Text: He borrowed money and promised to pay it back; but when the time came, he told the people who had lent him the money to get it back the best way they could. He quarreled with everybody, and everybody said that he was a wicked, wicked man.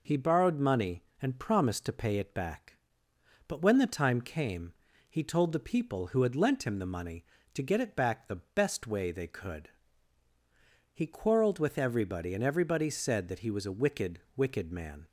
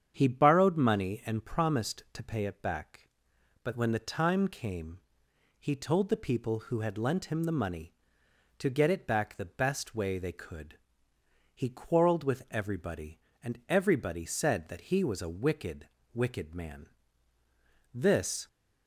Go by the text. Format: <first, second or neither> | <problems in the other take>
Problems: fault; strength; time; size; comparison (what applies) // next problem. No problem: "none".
first | starts louder than the rest; strong; until 1.1 s; 8 dB // goes on to say "This"; from 17.9 s on; 0.54 s long